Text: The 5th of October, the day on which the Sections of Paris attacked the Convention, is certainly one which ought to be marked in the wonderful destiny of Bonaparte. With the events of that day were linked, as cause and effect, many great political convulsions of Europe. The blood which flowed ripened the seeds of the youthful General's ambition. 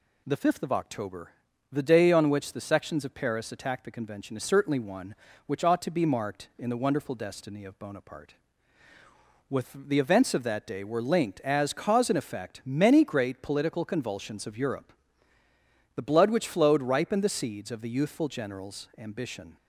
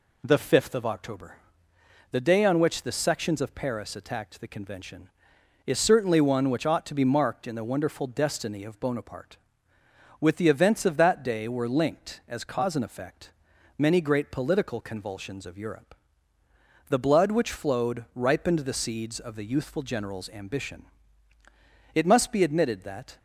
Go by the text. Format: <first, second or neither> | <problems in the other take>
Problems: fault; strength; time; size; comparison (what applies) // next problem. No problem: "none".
first | goes on to say "It must be admitted that"; noticeable; from 21.9 s on; 1.2 s long